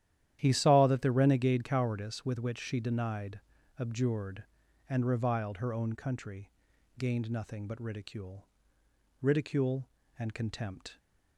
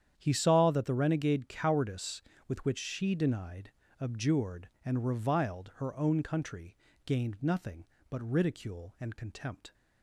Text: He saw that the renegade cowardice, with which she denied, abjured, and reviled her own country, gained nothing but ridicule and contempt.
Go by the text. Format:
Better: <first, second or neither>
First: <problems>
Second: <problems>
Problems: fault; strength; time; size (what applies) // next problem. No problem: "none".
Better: second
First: starts louder than the rest; strong; until 1.4 s; 11 dB // says "ridicule" twice; at 9.1 s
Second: starts louder than the rest; strong; until 1.1 s; 9 dB